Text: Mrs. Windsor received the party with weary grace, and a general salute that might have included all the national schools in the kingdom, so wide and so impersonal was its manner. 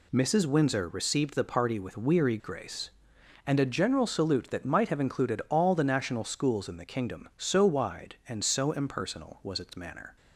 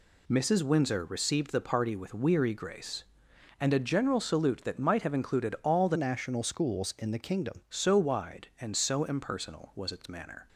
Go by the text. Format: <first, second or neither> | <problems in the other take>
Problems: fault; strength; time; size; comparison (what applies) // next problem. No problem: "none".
first | changes voice from "national" to "kingdom"; from 5.9 to 7.6 s; 1.7 s long